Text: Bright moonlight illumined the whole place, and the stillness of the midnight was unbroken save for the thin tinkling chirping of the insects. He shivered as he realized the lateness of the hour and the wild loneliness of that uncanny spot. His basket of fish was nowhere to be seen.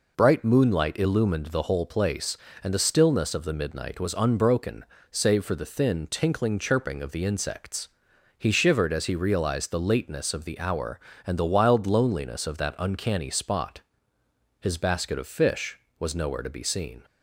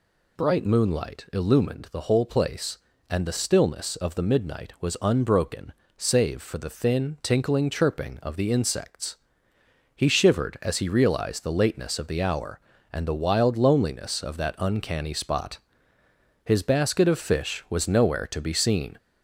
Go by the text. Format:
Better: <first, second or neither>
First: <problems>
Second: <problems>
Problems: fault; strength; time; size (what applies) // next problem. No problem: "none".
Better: first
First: pauses between "unbroken" and "save"; slight; at 4.8 s; 0.26 s long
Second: gets louder; slight; throughout; 2.5 dB // pauses between "unbroken" and "save"; slight; at 5.7 s; 0.24 s long